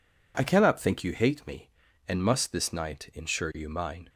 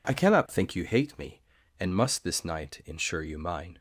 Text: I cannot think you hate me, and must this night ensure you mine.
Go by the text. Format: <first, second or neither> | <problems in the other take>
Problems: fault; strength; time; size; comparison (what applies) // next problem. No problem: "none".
neither | none